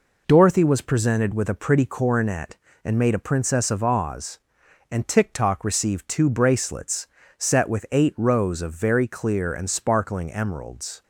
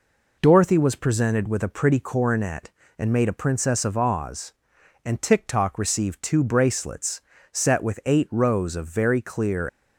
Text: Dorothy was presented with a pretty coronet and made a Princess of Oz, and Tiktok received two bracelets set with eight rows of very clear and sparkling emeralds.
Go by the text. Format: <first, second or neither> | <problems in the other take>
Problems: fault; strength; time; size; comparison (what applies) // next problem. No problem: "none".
first | pauses between "bracelets" and "set"; slight; at 7.2 s; 0.30 s long; slight in the first // stops before "and sparkling emeralds"; at 9.6 s